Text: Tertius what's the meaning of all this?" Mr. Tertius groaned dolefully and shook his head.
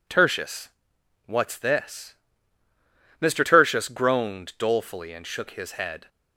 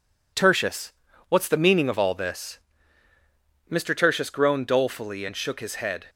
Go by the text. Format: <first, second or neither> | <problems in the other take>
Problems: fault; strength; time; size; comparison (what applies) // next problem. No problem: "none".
second | pauses between "Tertius" and "what's"; noticeable; at 0.6 s; 0.56 s long; slight in the second // skips "the meaning of all"; at 1.5 s